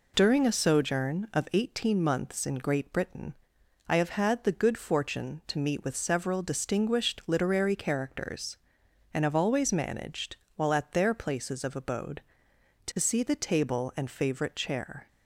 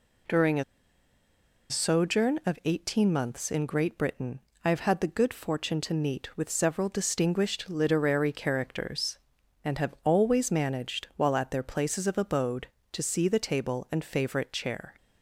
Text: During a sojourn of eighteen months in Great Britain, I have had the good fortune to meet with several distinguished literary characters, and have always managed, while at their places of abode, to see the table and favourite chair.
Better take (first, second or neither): first